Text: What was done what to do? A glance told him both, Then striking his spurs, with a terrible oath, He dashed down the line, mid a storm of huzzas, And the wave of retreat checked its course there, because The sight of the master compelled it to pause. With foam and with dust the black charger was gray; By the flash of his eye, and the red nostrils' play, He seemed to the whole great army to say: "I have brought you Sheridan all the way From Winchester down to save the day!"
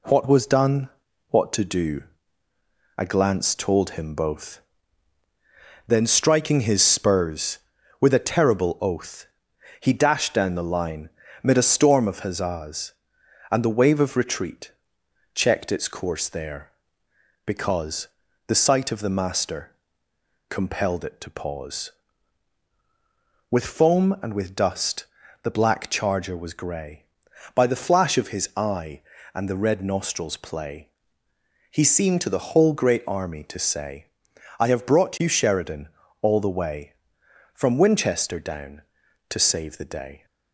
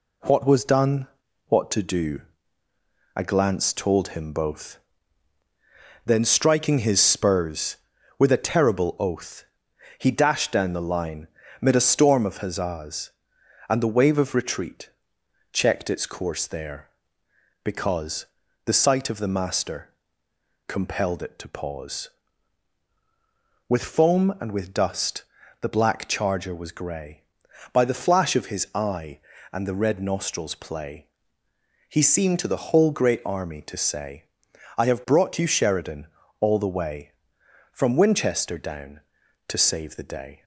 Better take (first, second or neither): neither